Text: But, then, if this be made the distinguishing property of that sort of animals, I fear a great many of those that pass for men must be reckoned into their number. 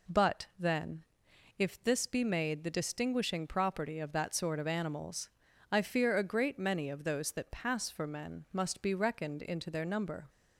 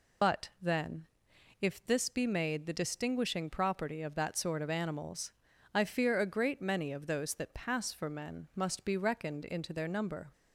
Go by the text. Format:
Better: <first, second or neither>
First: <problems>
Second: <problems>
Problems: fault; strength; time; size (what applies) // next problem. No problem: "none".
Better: first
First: none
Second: loses the start of "But"; at 0.2 s; 115 ms